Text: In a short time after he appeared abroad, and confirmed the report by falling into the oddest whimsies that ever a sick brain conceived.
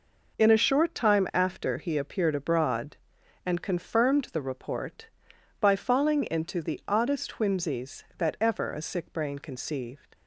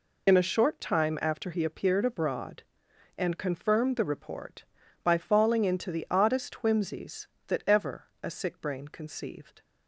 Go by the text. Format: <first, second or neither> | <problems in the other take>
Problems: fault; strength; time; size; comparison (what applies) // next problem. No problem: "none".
first | loses the start of "In"; at 0.2 s; 30 ms // pauses between "ever" and "a"; slight; at 8.0 s; 0.16 s long